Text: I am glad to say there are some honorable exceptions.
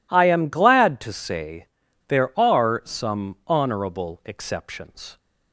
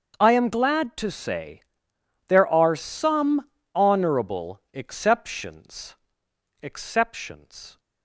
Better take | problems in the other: first | starts louder than the rest; until 1.2 s; 7 dB // pauses between "say" and "there"; noticeable; at 1.6 s; 0.68 s long; also in the first // pauses between "some" and "honorable"; slight; at 3.4 s; 0.28 s long // says "exceptions" twice; at 6.6 s

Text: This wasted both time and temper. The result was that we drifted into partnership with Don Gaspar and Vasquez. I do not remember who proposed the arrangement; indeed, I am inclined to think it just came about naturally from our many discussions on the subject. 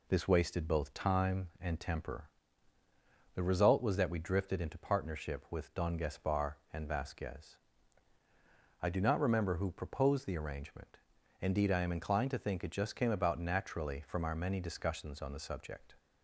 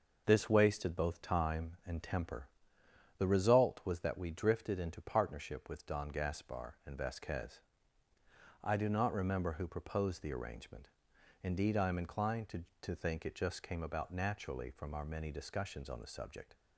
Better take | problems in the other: first | says "to" twice; at 12.8 s

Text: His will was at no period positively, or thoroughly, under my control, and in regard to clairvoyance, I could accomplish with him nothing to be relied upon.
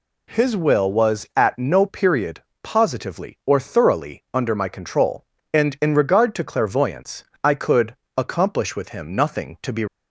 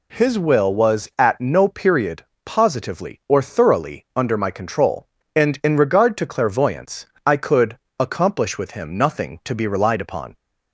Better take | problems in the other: second | pauses between "period" and "positively"; slight; at 2.4 s; 0.20 s long; slight in the second // pauses between "could" and "accomplish"; slight; at 7.9 s; 0.18 s long; slight in the second // stops before "relied upon"; at 9.8 s

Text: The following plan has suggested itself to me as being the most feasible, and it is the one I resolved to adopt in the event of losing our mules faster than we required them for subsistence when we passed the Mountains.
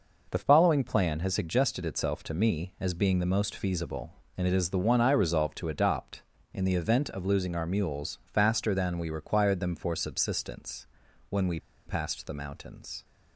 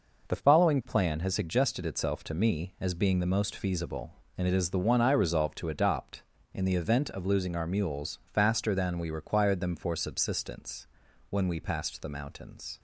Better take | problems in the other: second | pauses between "subsistence" and "when"; noticeable; at 10.8 s; 0.46 s long; noticeable in the second // pauses between "we" and "passed"; slight; at 11.5 s; 0.27 s long

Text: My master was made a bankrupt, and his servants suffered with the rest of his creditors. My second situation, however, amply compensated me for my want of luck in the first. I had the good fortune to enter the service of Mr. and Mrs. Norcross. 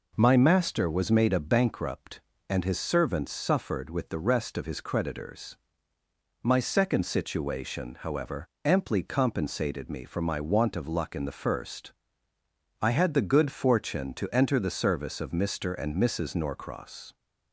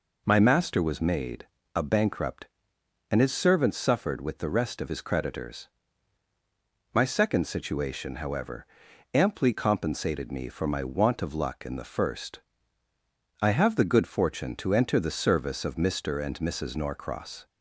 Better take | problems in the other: first | pauses between "made" and "a"; slight; at 1.4 s; 0.28 s long // says "have" for "had"; at 13.4 s

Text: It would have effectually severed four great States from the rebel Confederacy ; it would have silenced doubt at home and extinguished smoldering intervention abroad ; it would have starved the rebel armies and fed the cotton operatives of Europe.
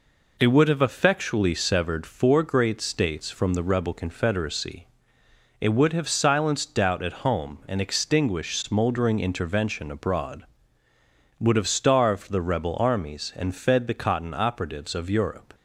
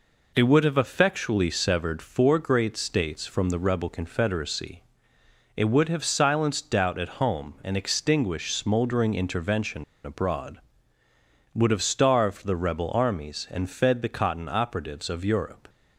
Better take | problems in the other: first | pauses between "intervention" and "abroad"; slight; at 9.8 s; 0.20 s long

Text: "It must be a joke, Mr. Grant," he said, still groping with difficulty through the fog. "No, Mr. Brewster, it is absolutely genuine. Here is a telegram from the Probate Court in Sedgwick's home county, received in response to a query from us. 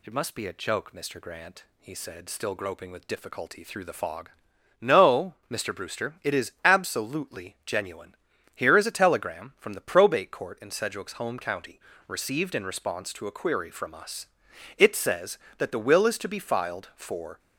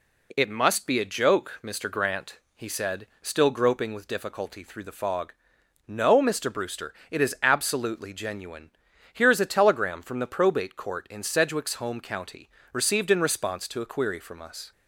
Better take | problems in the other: second | goes on to say "It says that the will is to be filed for"; strong; from 14.7 s on; 2.6 s long

